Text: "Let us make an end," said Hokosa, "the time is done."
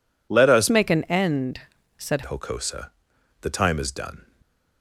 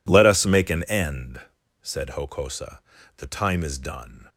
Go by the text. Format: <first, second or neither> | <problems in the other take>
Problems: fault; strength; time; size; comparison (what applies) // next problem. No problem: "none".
second | changes voice from "make" to "said"; from 0.7 to 2.2 s; 1.5 s long